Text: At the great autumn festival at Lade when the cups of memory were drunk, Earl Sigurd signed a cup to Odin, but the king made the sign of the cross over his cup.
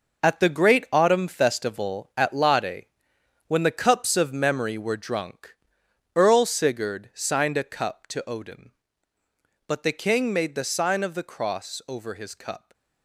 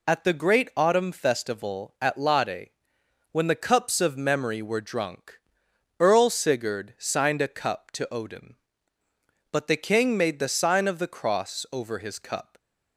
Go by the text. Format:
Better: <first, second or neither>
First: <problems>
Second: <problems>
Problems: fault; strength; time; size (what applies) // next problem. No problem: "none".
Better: second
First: gets quieter; strong; throughout; 10 dB // pauses between "Lade" and "when"; noticeable; at 2.8 s; 0.62 s long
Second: pauses between "Lade" and "when"; noticeable; at 2.6 s; 0.62 s long